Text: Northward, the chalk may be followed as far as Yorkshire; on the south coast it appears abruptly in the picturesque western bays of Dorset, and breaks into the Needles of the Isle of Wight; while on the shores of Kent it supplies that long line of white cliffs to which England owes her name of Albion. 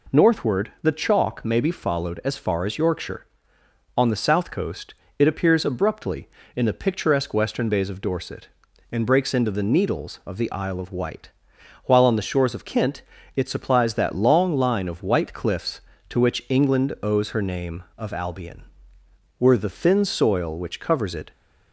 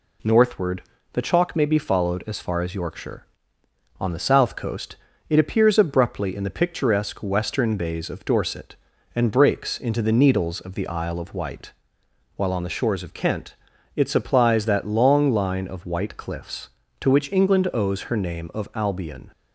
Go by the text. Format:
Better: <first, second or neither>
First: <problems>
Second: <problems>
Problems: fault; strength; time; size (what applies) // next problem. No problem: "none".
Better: second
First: pauses between "coast" and "it"; slight; at 4.9 s; 0.26 s long // pauses between "Kent" and "it"; slight; at 13.0 s; 0.34 s long // goes on to say "Were the thin soil which covers it"; strong; from 19.3 s on; 1.9 s long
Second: pauses between "coast" and "it"; slight; at 4.9 s; 0.36 s long // pauses between "Kent" and "it"; at 13.5 s; 0.40 s long